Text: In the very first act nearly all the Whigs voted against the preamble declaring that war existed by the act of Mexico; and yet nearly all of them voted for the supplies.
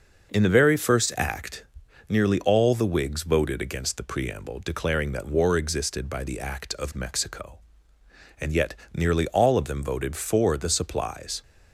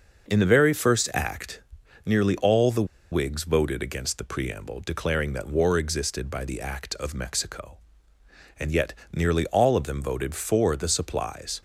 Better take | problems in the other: first | pauses between "act" and "nearly"; at 1.6 s; 0.44 s long; also in the first // pauses between "the" and "Whigs"; slight; at 2.8 s; 0.25 s long // pauses between "yet" and "nearly"; slight; at 8.9 s; 0.20 s long; slight in the first

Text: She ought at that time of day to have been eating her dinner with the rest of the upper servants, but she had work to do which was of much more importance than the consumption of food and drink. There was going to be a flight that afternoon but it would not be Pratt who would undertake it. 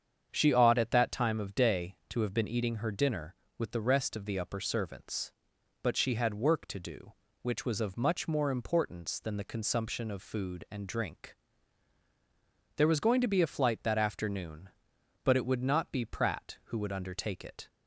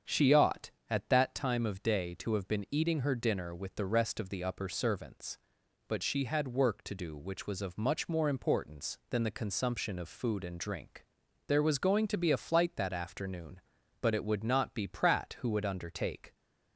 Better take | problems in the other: first | starts louder than the rest; strong; until 1.2 s; 7.5 dB; strong in the first // stops before "it"; at 16.3 s

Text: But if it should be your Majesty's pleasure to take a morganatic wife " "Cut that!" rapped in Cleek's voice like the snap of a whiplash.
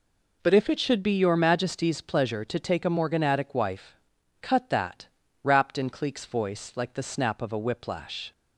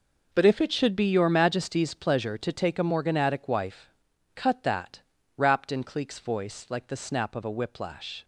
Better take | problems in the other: first | gets quieter; strong; throughout; 13 dB

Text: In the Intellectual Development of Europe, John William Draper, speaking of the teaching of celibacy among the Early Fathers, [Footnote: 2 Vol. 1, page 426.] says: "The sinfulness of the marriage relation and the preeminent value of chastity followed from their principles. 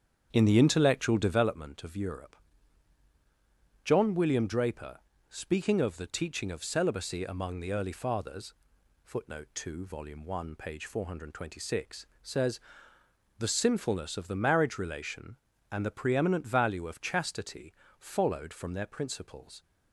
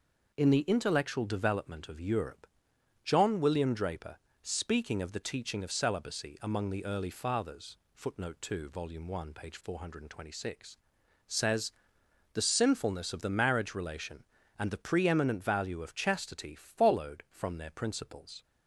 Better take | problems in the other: second | starts louder than the rest; strong; until 1.4 s; 8 dB // pauses between "chastity" and "followed"; slight; at 17.7 s; 0.26 s long

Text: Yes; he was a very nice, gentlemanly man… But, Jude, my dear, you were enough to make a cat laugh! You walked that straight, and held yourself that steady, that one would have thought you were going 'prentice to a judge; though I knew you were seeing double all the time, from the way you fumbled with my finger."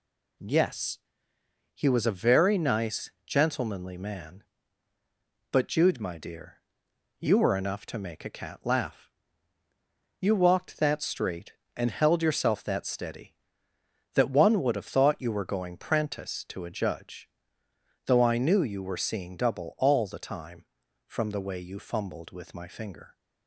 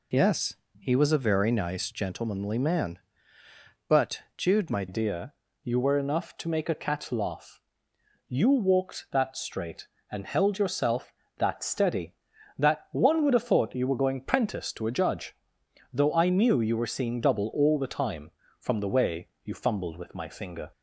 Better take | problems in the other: first | changes voice at "dear"; from 4.8 s on; 15.9 s long // pauses between "way" and "you"; slight; at 19.2 s; 0.16 s long

